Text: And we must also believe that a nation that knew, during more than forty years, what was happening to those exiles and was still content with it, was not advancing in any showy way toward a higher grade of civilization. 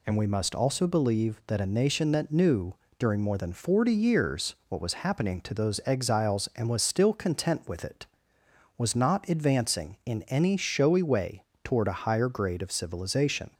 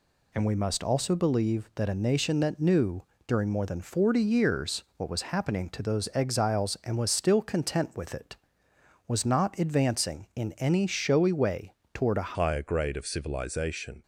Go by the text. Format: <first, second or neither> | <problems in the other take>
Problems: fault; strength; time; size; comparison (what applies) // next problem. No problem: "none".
first | pauses between "way" and "toward"; slight; at 11.7 s; 0.20 s long; slight in the first // changes voice at "higher"; from 12.3 s on; 1.7 s long